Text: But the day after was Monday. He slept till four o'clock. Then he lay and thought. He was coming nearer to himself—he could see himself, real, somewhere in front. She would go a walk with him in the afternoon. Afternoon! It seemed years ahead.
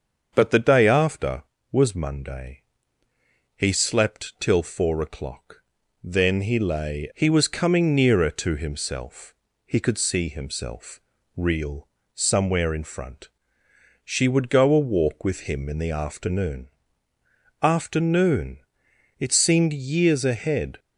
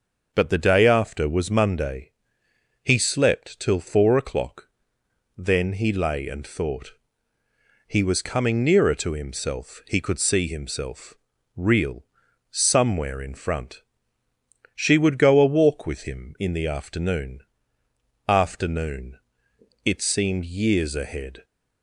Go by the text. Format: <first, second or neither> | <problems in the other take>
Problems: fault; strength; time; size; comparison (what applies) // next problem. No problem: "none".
second | starts louder than the rest; until 1.3 s; 7 dB // skips "and thought"; at 7.1 s